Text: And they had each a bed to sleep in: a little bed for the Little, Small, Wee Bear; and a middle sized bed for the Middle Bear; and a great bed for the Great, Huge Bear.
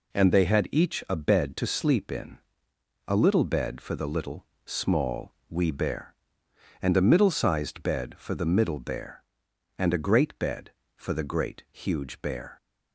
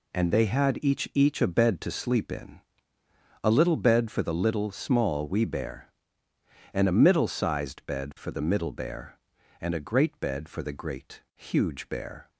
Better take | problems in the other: first | says "each" twice; at 1.1 s

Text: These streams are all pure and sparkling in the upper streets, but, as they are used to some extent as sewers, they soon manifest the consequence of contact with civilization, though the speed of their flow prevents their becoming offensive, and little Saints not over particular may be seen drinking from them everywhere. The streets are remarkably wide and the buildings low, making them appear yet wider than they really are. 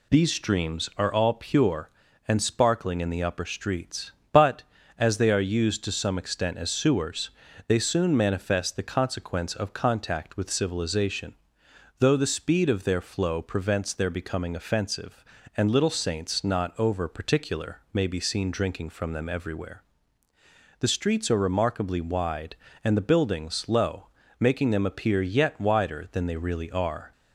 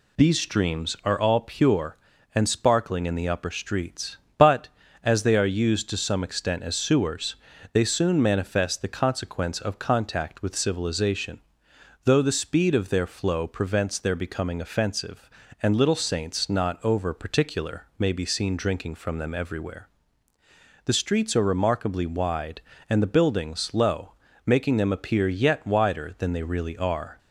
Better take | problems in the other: neither | none

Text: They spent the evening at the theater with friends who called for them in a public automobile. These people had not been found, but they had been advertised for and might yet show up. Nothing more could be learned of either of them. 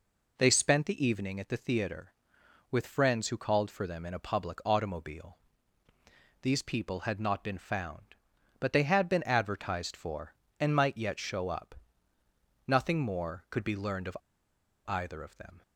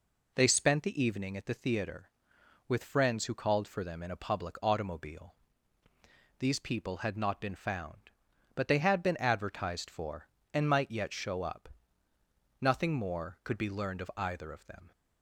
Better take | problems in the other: second | pauses between "of" and "either"; noticeable; at 14.1 s; 0.68 s long

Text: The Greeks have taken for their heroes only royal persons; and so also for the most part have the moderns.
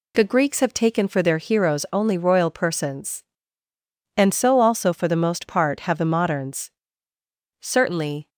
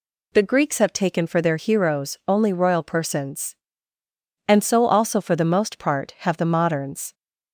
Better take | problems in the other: second | goes on to say "Certainly"; noticeable; from 7.6 s on; 0.66 s long

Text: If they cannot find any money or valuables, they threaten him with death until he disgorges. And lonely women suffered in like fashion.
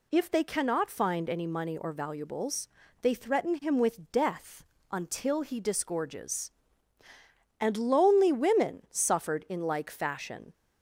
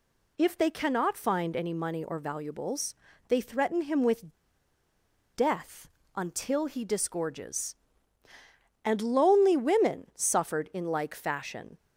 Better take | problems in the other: first | pauses between "with" and "death"; at 4.3 s; 1.0 s long // pauses between "death" and "until"; slight; at 5.8 s; 0.26 s long; slight in the first

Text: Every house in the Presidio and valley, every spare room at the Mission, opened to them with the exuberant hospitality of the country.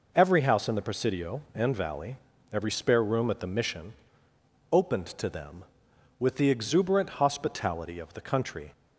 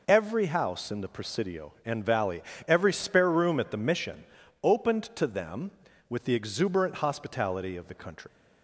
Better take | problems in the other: first | leaves "country" unfinished; at 8.2 s; 135 ms

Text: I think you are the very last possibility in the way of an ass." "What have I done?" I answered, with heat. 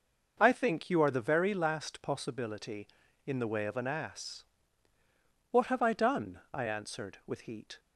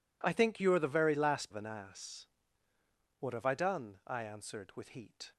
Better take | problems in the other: first | skips "possibility in the way"; at 1.5 s

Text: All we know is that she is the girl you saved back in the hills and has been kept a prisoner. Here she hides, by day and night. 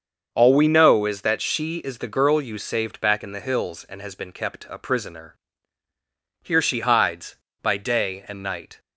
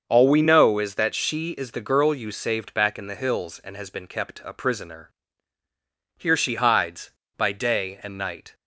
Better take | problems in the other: neither | starts louder than the rest; the same in both

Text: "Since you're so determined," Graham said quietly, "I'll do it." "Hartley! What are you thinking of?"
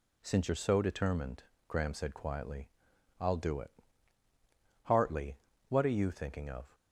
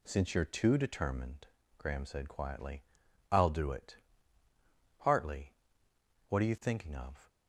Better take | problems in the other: first | says "too" for "so"; at 0.4 s

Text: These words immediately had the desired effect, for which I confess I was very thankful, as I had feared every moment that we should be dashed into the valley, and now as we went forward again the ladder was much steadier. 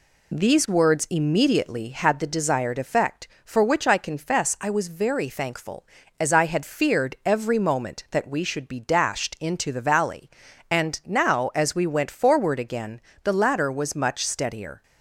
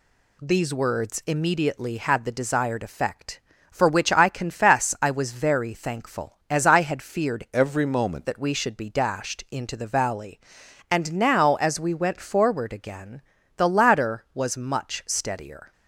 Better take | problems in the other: first | changes voice from "every" to "moment"; from 7.5 to 8.2 s; 0.7 s long // pauses between "again" and "the"; slight; at 13.2 s; 0.34 s long; slight in the first

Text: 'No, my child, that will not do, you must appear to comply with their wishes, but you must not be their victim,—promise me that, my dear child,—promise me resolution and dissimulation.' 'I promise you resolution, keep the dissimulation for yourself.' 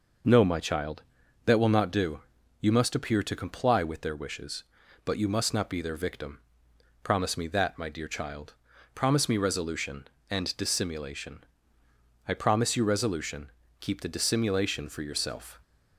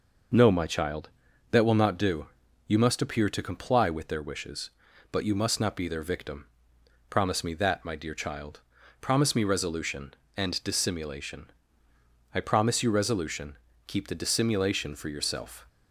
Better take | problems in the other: neither | none

